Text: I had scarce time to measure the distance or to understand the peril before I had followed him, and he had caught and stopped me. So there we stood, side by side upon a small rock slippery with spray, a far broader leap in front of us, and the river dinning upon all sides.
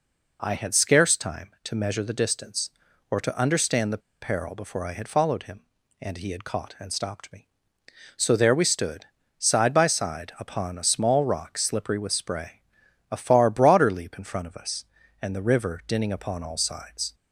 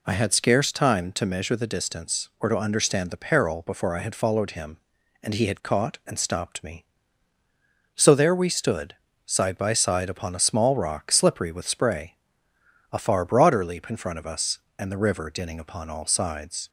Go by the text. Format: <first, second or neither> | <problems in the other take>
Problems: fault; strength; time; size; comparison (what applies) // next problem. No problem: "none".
second | pauses between "the" and "peril"; slight; at 4.0 s; 0.22 s long